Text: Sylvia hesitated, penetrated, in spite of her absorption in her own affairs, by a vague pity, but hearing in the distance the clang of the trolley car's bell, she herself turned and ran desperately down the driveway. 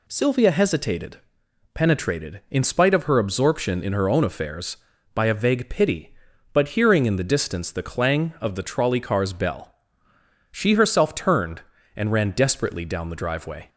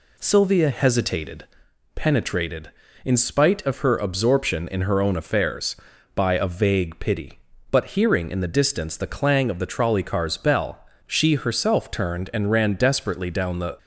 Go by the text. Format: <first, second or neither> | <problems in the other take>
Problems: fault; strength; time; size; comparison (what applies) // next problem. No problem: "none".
first | stops before "driveway"; at 13.7 s